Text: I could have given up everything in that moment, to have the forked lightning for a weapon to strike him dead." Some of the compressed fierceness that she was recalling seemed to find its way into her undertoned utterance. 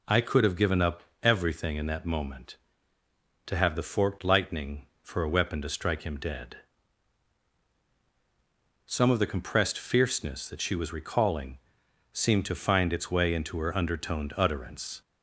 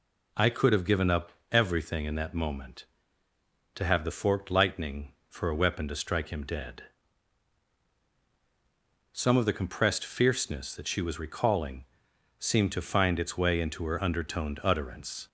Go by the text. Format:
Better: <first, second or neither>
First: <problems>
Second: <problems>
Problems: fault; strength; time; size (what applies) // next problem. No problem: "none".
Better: neither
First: pauses between "up" and "everything"; slight; at 1.0 s; 0.20 s long // pauses between "recalling" and "seemed"; noticeable; at 11.5 s; 0.56 s long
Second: pauses between "up" and "everything"; slight; at 1.3 s; 0.20 s long // pauses between "recalling" and "seemed"; noticeable; at 11.8 s; 0.56 s long